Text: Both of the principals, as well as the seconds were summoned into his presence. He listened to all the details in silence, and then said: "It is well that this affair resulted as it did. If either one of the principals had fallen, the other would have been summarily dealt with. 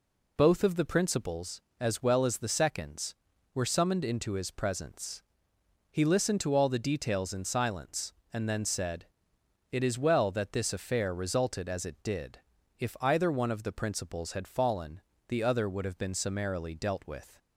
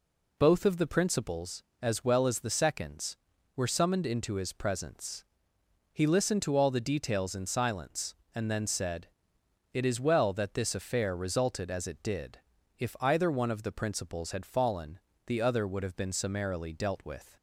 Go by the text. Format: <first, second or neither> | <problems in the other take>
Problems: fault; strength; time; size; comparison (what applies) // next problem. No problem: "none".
neither | none